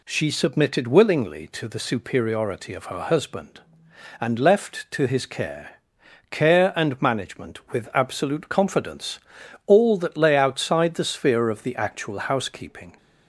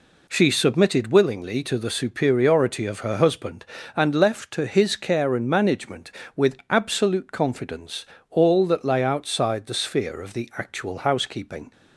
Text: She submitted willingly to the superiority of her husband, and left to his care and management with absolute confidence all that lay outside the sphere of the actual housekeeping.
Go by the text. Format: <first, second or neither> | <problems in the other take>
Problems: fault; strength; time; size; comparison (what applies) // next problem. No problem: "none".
second | says "care" twice; at 6.3 s // pauses between "confidence" and "all"; noticeable; at 9.1 s; 0.48 s long; slight in the second